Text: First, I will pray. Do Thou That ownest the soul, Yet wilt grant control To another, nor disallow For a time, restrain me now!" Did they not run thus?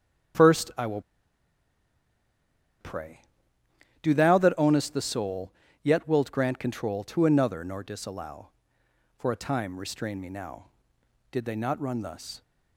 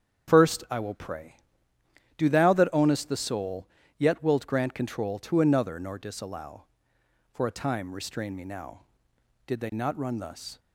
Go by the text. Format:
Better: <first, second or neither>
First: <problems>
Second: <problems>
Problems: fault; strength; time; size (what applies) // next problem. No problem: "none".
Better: second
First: starts louder than the rest; strong; until 4.0 s; 8 dB // pauses between "will" and "pray"; strong; at 0.9 s; 1.8 s long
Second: starts louder than the rest; strong; until 1.3 s; 8 dB